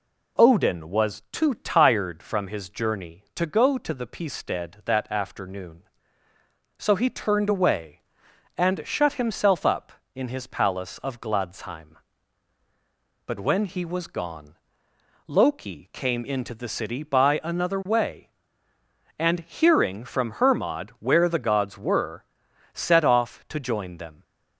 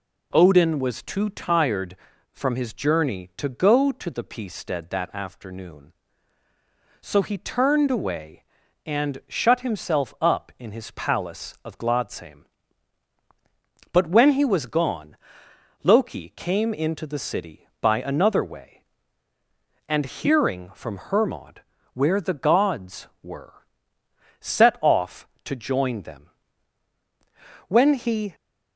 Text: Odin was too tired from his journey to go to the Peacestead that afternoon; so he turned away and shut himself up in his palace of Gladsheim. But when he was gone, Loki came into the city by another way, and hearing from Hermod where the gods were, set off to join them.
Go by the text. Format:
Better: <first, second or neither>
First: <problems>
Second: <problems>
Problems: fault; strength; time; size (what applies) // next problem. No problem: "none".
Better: first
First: none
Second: pauses between "Hermod" and "where"; slight; at 21.6 s; 0.32 s long // goes on to say "When he"; noticeable; from 27.6 s on; 0.68 s long